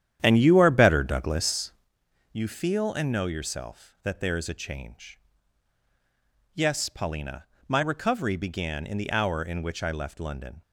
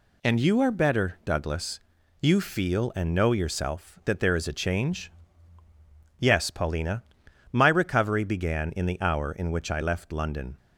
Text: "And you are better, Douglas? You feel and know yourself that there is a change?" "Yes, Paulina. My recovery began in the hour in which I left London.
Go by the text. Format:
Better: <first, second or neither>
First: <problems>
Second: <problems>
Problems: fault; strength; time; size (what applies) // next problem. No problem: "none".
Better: second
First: starts louder than the rest; strong; until 1.9 s; 10 dB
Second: none